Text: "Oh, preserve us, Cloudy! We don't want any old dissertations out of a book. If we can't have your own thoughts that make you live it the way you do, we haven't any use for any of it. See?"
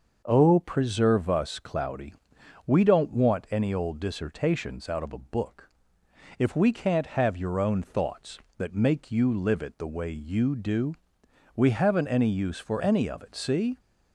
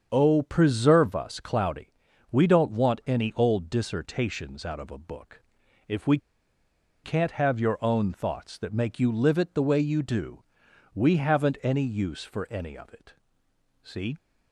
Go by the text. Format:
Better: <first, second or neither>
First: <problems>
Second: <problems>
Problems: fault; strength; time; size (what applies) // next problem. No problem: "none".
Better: first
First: none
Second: starts louder than the rest; strong; until 1.1 s; 7 dB // pauses between "we" and "can't"; noticeable; at 6.1 s; 0.86 s long